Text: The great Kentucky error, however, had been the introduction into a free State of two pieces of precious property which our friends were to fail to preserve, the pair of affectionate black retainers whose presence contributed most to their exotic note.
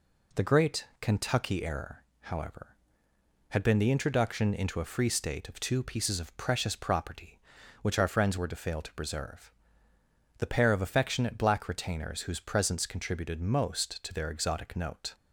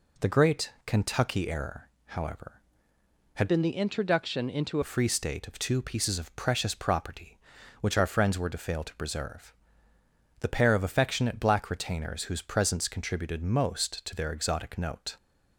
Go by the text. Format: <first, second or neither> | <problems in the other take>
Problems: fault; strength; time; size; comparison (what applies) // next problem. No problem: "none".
first | pauses between "great" and "Kentucky"; slight; at 0.7 s; 0.16 s long; slight in the first // changes voice from "been" to "into"; from 3.4 to 4.8 s; 1.4 s long